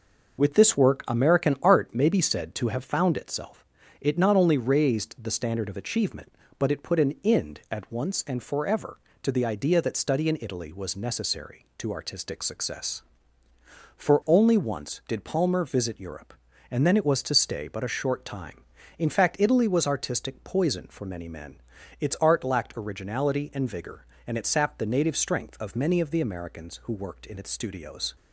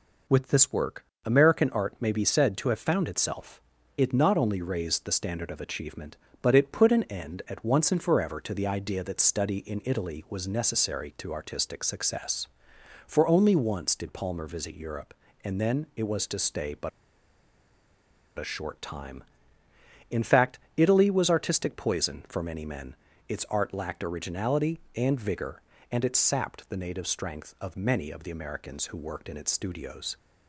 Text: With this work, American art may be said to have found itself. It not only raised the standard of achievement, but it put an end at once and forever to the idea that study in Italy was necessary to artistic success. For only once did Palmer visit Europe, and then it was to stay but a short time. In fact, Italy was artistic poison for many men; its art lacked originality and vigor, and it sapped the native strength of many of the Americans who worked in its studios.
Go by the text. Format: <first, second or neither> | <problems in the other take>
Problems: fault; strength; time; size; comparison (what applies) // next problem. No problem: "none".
first | pauses between "but" and "a"; strong; at 16.9 s; 1.4 s long